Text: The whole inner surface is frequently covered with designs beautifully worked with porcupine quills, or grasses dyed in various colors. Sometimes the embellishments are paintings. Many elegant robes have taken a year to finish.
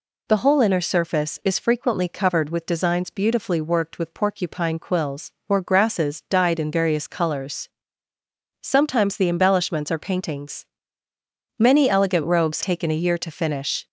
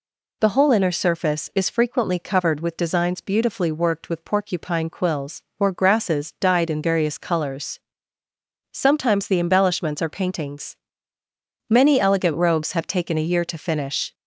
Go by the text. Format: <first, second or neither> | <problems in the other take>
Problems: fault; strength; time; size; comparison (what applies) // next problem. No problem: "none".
second | skips "have"; at 12.6 s